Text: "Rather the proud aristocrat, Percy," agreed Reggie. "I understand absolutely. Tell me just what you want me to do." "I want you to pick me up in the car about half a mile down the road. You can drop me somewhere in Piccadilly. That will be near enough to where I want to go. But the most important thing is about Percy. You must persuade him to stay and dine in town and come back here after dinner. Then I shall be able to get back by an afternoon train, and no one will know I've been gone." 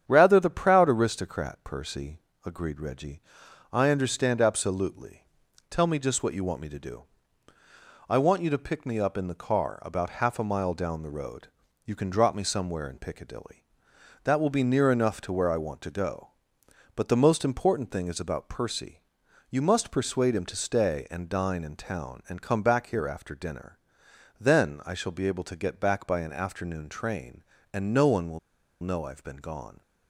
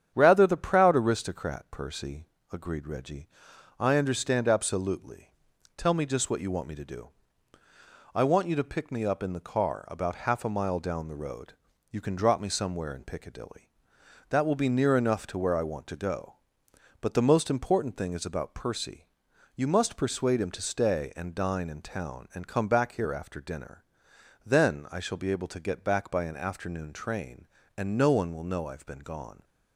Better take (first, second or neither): second